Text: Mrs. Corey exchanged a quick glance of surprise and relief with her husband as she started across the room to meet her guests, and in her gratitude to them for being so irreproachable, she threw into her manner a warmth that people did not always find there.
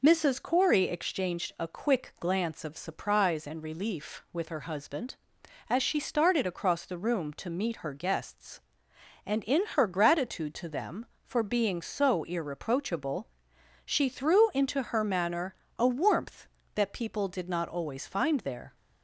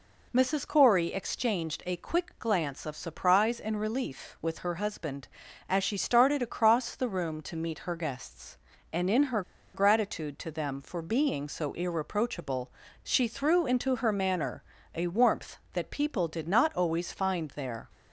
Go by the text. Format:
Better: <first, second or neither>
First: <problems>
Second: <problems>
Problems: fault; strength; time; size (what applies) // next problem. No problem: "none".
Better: first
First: pauses between "manner" and "a"; slight; at 15.5 s; 0.24 s long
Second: pauses between "her" and "gratitude"; slight; at 9.4 s; 0.33 s long // pauses between "manner" and "a"; slight; at 14.6 s; 0.32 s long